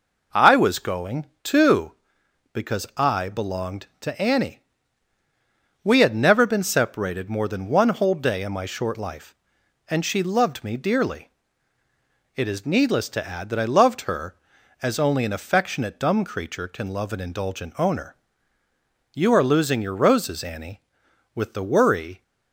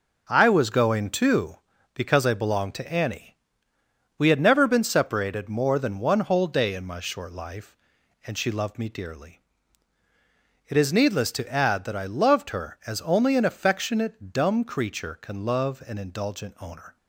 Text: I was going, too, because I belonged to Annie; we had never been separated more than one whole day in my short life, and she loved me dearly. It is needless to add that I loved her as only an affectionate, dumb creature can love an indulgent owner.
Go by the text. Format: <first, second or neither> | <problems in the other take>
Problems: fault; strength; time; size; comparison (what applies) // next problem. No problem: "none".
second | goes on to say "You are losing your roses Annie with the worry"; strong; from 19.1 s on; 3.1 s long